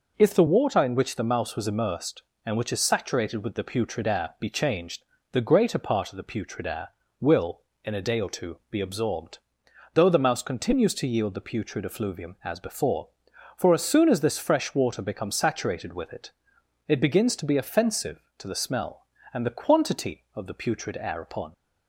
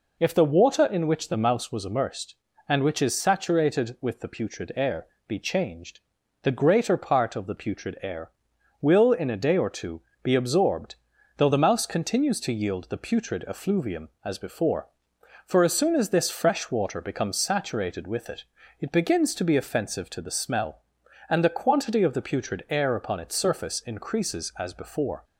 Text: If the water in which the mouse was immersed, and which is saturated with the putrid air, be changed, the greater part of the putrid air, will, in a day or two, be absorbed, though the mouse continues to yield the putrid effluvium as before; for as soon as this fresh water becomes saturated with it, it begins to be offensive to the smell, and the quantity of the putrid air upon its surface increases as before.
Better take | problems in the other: second | stops before "its surface increases as before"; at 21.5 s

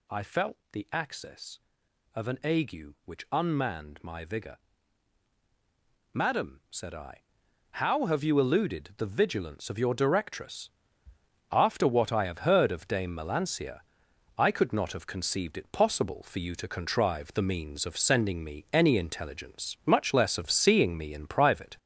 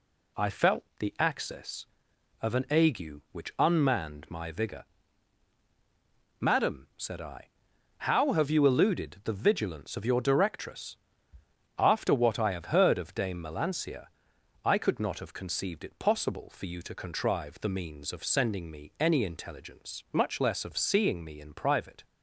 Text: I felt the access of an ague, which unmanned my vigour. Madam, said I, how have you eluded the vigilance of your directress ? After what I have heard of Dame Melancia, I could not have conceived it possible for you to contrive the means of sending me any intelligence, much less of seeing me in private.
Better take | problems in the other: second | gets louder; noticeable; throughout; 4.5 dB // pauses between "felt" and "the"; slight; at 0.5 s; 0.16 s long; slight in the second

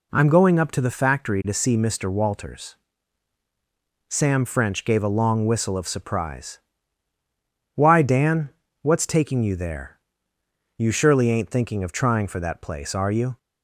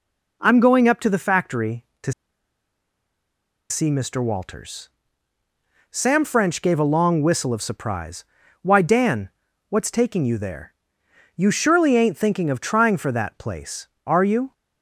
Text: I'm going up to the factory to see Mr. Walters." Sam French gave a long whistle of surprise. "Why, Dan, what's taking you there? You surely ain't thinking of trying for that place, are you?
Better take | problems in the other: first | pauses between "to" and "see"; strong; at 2.1 s; 1.5 s long

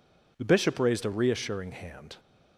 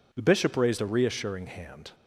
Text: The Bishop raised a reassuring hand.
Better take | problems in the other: neither | none

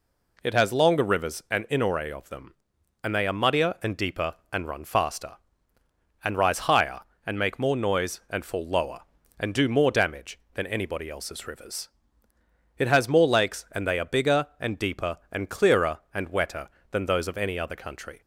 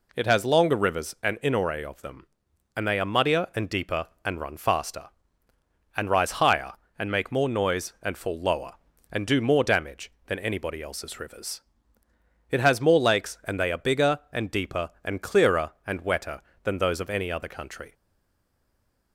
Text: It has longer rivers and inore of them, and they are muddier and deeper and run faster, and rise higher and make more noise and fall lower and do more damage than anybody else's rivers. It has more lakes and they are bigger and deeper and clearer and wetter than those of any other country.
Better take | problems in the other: first | stays silent after the last word; noticeable; from 17.9 s on; 1.2 s long

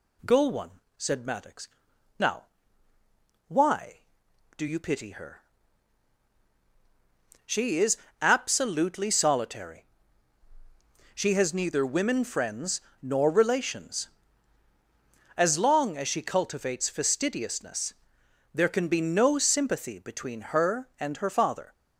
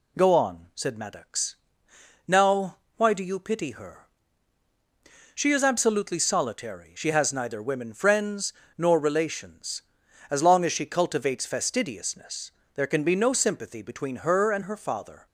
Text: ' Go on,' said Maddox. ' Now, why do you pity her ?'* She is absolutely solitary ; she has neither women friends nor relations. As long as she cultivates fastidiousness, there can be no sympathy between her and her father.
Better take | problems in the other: second | says "one" for "on"; at 0.4 s // pauses between "is" and "absolutely"; slight; at 7.9 s; 0.24 s long // pauses between "friends" and "nor"; slight; at 12.8 s; 0.20 s long; slight in the second

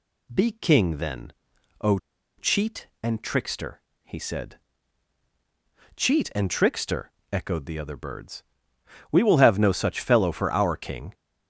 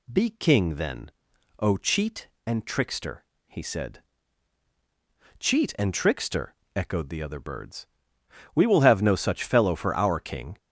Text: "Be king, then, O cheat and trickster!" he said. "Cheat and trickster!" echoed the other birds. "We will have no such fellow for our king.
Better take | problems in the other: second | pauses between "O" and "cheat"; at 1.9 s; 0.40 s long

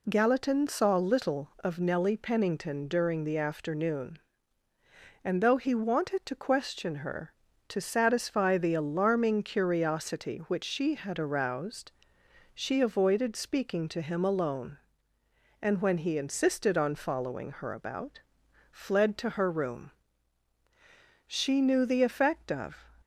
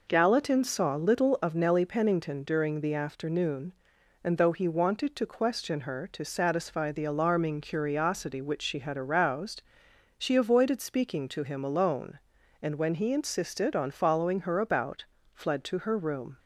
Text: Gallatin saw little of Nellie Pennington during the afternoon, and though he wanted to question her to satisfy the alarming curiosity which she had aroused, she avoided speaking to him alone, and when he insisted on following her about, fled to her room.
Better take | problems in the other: second | goes on to say "She knew the effect of"; from 21.2 s on; 1.5 s long

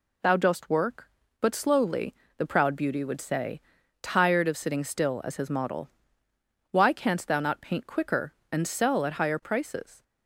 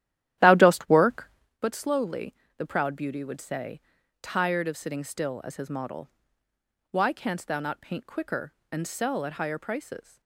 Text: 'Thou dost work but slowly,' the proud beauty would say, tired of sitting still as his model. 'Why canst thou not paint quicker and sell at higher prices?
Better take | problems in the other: first | starts louder than the rest; strong; until 1.6 s; 12.5 dB

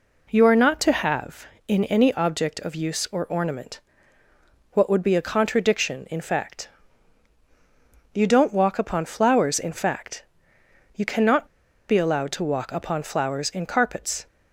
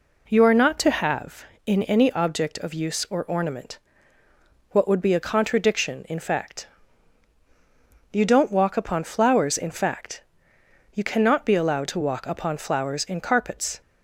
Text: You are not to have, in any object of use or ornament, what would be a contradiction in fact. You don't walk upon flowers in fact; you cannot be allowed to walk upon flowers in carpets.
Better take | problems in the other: second | pauses between "cannot" and "be"; at 11.4 s; 0.41 s long

